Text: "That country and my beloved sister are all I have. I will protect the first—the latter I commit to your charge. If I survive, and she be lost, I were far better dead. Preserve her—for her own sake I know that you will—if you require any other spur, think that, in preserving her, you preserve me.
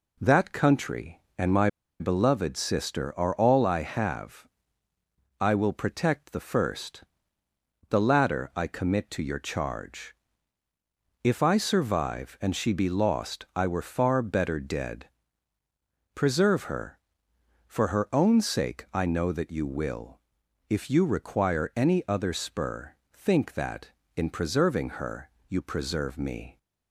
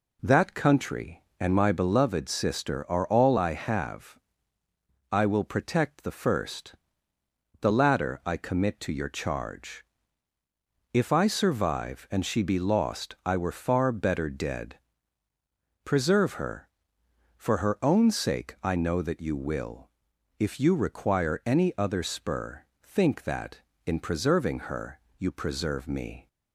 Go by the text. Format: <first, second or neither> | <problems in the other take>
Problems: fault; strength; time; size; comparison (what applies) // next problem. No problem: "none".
second | pauses between "my" and "beloved"; slight; at 1.6 s; 0.30 s long